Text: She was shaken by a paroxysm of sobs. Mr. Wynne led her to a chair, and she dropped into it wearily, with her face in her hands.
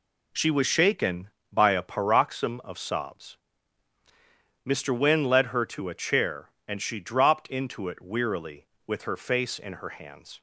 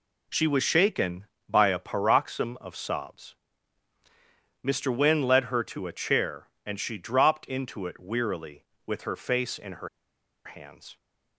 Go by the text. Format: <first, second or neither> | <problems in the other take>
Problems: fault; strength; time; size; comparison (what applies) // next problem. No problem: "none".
first | pauses between "her" and "hands"; noticeable; at 9.8 s; 0.57 s long